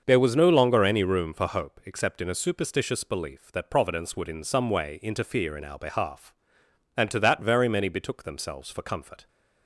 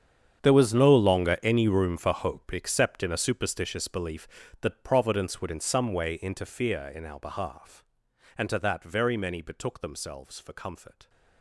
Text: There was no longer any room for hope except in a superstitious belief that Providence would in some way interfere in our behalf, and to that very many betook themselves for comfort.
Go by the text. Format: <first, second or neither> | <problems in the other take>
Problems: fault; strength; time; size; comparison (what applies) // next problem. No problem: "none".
first | gets quieter; strong; throughout; 17.5 dB // starts louder than the rest; strong; until 1.5 s; 8.5 dB; also in the first